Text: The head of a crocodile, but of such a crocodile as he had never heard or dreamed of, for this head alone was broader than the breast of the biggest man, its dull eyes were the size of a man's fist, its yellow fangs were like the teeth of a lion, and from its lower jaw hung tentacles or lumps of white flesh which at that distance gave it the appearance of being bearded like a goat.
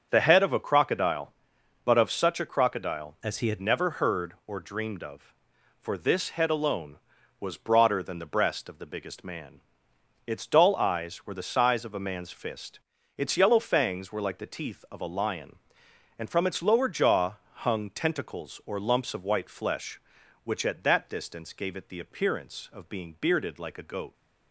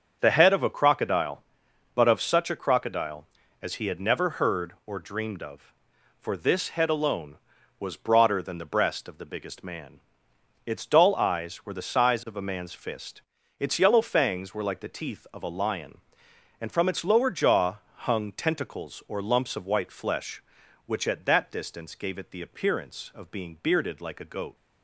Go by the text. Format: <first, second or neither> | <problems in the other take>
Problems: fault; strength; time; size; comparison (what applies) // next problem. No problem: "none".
second | starts louder than the rest; until 1.1 s; 7 dB; also in the second // changes voice from "as" to "had"; from 3.2 to 3.5 s; 0.3 s long // pauses between "jaw" and "hung"; slight; at 17.3 s; 0.16 s long; slight in the second